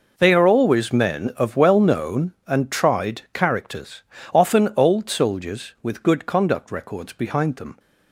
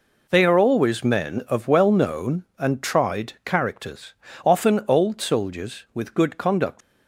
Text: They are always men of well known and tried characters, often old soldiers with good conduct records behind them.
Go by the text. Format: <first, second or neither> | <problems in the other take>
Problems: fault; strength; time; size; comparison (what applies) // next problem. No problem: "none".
first | stops before "records behind them"; at 6.8 s